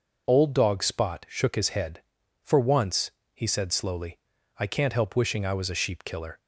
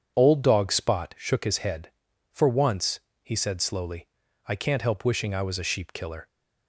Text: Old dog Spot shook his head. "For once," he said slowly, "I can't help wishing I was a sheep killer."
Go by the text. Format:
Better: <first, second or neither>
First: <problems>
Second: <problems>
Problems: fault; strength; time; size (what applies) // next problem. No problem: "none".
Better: first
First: none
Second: starts louder than the rest; strong; until 1.2 s; 7.5 dB